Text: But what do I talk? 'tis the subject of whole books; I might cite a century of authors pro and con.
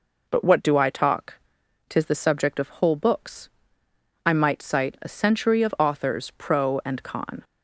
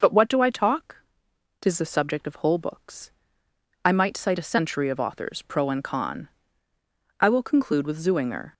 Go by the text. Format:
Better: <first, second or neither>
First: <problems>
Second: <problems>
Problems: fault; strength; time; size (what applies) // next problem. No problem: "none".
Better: first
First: none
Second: goes on to say "I will conclude with Zuinger"; from 7.1 s on; 1.3 s long